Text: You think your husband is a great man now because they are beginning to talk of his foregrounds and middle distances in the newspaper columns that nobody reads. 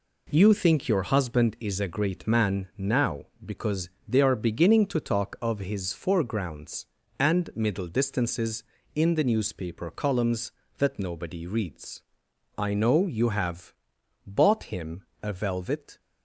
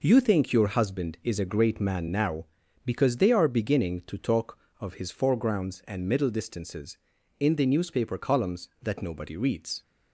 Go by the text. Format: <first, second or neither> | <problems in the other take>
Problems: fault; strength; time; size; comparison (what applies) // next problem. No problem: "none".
second | pauses between "because" and "they"; slight; at 3.8 s; 0.20 s long // goes on to say "I know you have bought him a velvet"; strong; from 12.5 s on; 3.4 s long